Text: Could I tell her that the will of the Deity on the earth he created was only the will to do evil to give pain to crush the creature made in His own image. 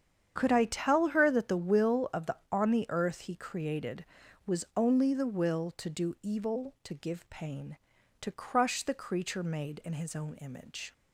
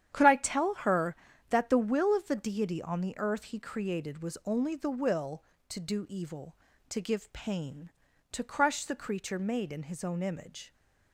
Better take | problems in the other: second | starts louder than the rest; strong; until 1.3 s; 8.5 dB; strong in the second // skips "Deity"; at 2.4 s

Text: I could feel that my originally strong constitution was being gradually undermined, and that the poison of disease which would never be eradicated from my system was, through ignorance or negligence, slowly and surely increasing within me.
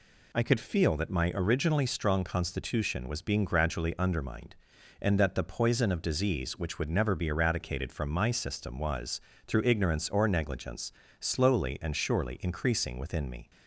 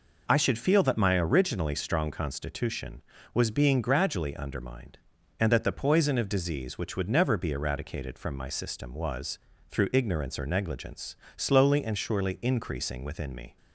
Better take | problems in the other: first | says "should" for "could"; at 0.3 s

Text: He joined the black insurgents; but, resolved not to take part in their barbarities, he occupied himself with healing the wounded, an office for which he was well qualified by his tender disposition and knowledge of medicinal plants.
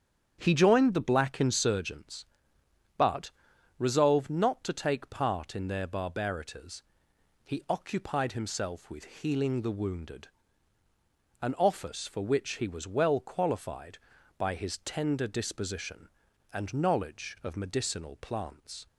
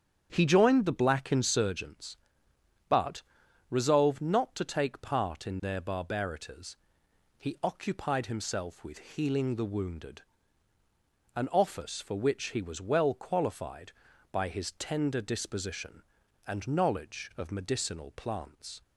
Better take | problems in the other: neither | starts louder than the rest; strong; the same in both

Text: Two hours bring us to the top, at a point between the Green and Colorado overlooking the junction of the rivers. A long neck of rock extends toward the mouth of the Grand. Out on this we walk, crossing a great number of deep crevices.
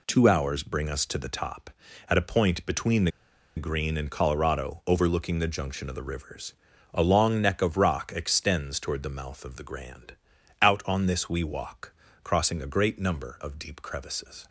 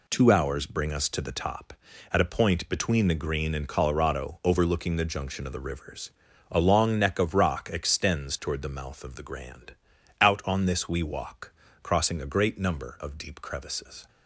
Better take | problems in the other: second | pauses between "the" and "Green"; noticeable; at 3.1 s; 0.46 s long

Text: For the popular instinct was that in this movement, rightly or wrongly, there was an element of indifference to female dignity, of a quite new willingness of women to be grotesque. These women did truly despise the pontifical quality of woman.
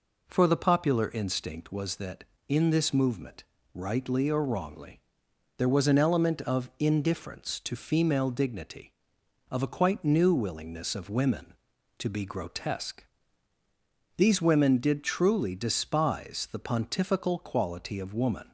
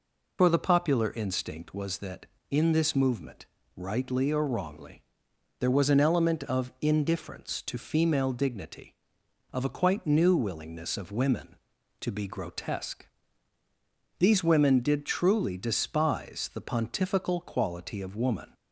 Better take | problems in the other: first | loses the start of "For"; at 0.3 s; 95 ms

